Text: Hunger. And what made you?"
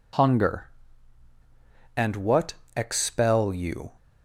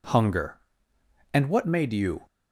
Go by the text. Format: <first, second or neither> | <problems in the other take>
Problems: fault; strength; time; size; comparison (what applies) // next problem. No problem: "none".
second | says "expel" for "made"; at 2.7 s